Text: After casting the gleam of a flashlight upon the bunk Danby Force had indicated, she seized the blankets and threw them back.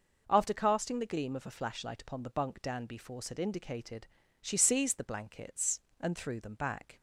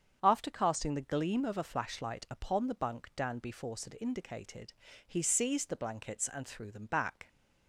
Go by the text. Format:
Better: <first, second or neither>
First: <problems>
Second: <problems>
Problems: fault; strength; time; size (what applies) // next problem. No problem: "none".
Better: first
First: none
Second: starts louder than the rest; strong; until 1.2 s; 7.5 dB // says "he" for "she"; at 5.0 s